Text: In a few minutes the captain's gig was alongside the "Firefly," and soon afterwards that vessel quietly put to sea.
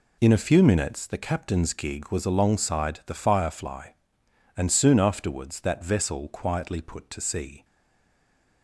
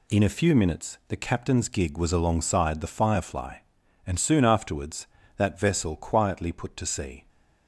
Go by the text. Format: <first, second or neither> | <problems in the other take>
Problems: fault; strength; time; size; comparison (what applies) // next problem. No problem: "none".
second | stays silent after the last word; from 7.6 s on; 1.0 s long